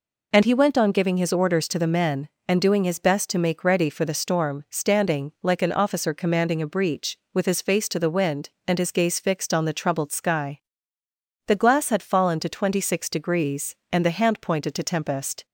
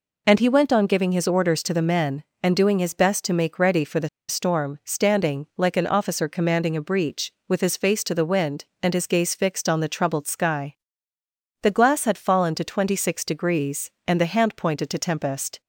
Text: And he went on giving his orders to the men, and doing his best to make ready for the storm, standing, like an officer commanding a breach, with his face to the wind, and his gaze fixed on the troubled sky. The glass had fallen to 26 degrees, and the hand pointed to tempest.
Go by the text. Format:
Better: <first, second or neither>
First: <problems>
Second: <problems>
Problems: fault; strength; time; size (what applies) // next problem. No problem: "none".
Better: first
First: none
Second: pauses between "the" and "storm"; slight; at 4.0 s; 0.20 s long